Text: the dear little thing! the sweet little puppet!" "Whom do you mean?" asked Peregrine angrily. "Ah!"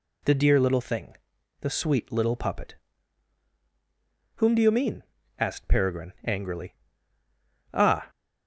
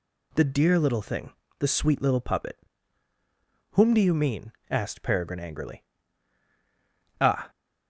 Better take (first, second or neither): neither